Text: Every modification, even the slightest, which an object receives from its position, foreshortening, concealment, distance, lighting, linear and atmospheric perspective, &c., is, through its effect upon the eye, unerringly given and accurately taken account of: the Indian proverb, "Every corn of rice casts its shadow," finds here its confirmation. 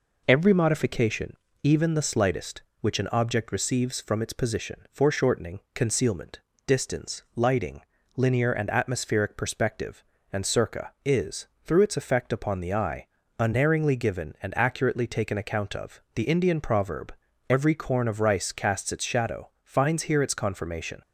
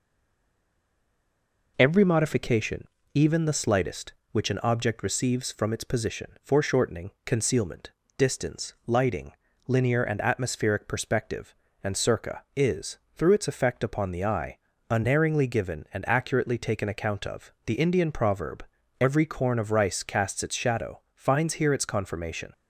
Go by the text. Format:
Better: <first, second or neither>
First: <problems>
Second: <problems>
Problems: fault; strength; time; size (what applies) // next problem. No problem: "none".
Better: first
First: none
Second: stays silent before the first word; noticeable; until 1.7 s; 1.7 s long